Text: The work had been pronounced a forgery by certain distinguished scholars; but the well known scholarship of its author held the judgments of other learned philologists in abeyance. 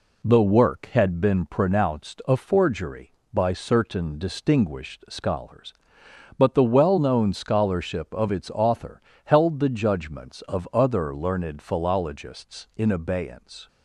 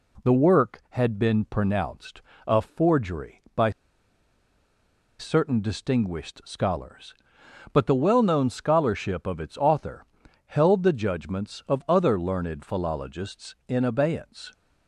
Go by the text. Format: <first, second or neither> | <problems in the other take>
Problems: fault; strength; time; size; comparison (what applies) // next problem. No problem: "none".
first | pauses between "pronounced" and "a"; slight; at 2.2 s; 0.26 s long // pauses between "by" and "certain"; strong; at 3.7 s; 1.4 s long // pauses between "author" and "held"; at 10.0 s; 0.42 s long; slight in the first